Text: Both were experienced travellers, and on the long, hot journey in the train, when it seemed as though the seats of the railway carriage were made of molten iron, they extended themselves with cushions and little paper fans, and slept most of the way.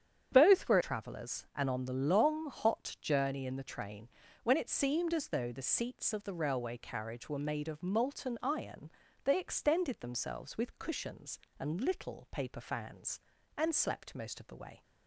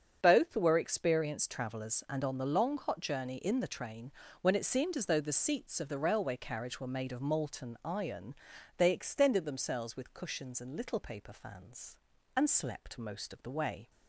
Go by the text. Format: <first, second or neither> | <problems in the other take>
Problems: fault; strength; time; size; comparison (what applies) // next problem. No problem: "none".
second | starts louder than the rest; strong; until 1.3 s; 8.5 dB; strong in the second // skips "experienced"; at 0.8 s